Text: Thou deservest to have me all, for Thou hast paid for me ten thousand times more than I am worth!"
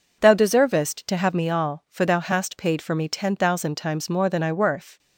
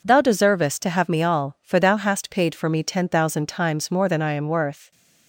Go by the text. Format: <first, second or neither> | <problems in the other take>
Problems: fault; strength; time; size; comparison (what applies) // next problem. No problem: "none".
second | skips "am"; at 4.5 s